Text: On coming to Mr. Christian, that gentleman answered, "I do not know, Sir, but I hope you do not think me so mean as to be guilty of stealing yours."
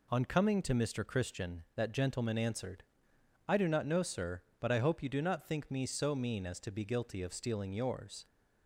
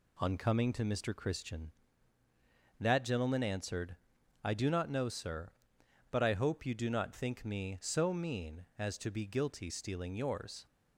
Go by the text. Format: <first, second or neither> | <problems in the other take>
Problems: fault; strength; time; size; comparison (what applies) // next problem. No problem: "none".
first | skips "of"; at 9.6 s